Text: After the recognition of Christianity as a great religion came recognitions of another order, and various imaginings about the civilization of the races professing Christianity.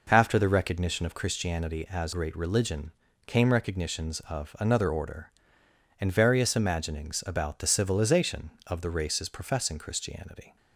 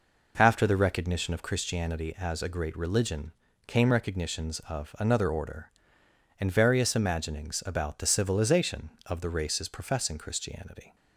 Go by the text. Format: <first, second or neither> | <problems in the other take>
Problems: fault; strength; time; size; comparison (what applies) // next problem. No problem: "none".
second | skips "a"; at 2.1 s // pauses between "religion" and "came"; slight; at 2.9 s; 0.34 s long; slight in the second